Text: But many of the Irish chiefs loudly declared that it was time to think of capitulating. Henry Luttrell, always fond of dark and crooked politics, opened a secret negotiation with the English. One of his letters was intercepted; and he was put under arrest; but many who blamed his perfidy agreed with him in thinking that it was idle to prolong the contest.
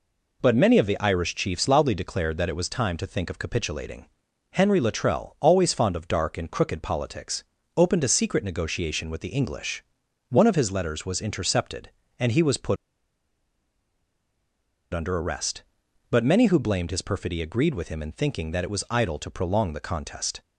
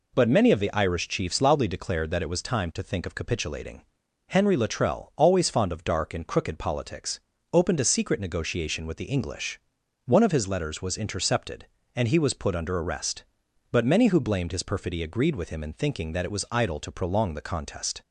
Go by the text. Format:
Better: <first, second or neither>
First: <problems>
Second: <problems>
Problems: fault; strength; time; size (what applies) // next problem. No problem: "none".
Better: second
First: pauses between "put" and "under"; strong; at 12.7 s; 2.1 s long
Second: none